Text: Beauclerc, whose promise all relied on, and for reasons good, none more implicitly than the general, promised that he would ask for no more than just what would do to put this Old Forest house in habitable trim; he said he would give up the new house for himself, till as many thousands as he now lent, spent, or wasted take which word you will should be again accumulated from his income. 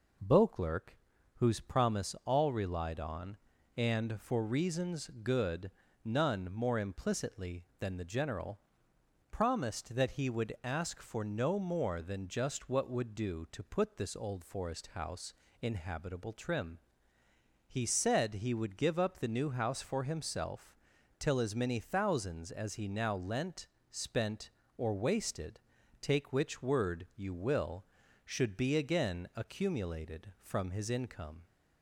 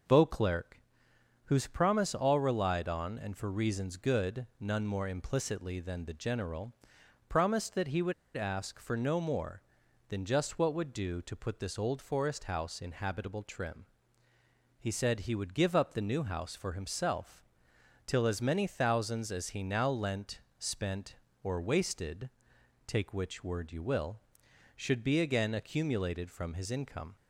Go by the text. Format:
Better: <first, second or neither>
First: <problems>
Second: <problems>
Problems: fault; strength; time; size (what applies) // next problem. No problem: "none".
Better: first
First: pauses between "wasted" and "take"; at 25.5 s; 0.44 s long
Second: pauses between "would" and "ask"; slight; at 8.1 s; 0.24 s long // pauses between "wasted" and "take"; noticeable; at 22.2 s; 0.56 s long